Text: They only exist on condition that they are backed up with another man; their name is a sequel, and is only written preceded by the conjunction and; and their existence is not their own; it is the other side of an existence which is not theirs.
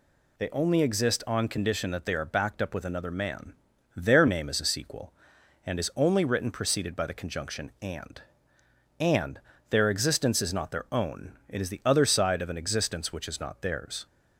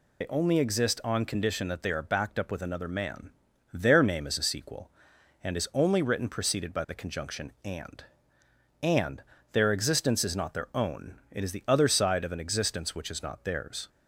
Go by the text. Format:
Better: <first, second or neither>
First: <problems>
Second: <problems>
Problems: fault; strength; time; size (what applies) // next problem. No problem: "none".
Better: first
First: pauses between "and" and "their"; slight; at 9.4 s; 0.26 s long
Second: loses the start of "They"; at 0.2 s; 55 ms // pauses between "and" and "their"; slight; at 9.2 s; 0.26 s long